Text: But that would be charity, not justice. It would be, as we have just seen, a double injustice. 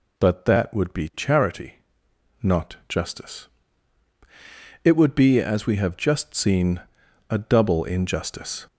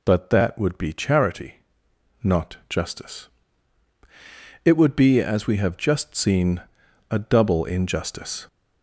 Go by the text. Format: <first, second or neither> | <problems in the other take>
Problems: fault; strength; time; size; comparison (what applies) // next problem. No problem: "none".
neither | none